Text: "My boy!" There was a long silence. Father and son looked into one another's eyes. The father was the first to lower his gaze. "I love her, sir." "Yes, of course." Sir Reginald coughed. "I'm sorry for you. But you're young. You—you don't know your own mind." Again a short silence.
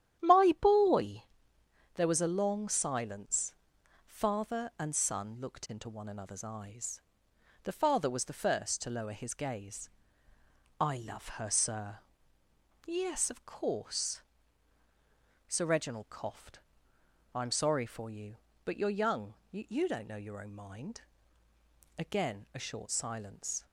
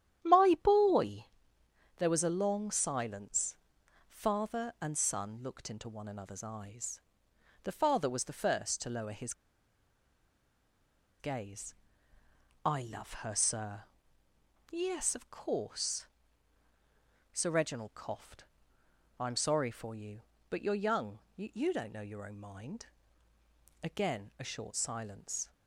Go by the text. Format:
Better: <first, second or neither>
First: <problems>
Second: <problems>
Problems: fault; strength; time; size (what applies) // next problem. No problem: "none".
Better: first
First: starts louder than the rest; strong; until 1.9 s; 10.5 dB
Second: starts louder than the rest; strong; until 1.9 s; 10.5 dB // pauses between "his" and "gaze"; strong; at 9.3 s; 1.8 s long